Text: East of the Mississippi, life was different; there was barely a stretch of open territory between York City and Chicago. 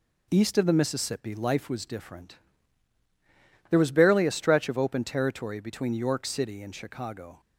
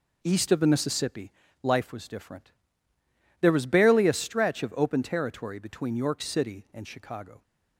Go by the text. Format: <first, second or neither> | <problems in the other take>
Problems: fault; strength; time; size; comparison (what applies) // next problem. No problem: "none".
neither | none